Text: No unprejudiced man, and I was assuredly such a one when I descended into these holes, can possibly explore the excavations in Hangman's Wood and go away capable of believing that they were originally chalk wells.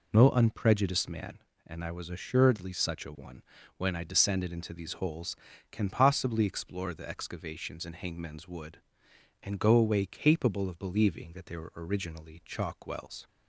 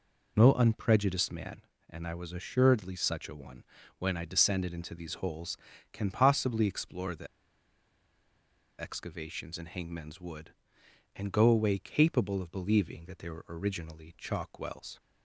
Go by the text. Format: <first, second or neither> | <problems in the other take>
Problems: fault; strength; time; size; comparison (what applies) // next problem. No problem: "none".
first | pauses between "one" and "when"; slight; at 3.6 s; 0.36 s long; slight in the first // pauses between "the" and "excavations"; strong; at 7.2 s; 1.5 s long